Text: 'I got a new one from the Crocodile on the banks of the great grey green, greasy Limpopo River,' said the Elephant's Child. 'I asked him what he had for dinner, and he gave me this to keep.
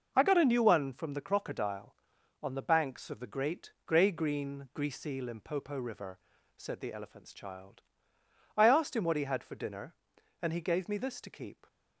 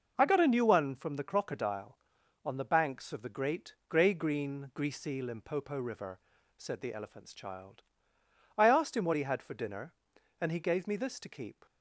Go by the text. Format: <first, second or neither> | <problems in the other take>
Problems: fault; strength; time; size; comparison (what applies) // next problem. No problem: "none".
neither | none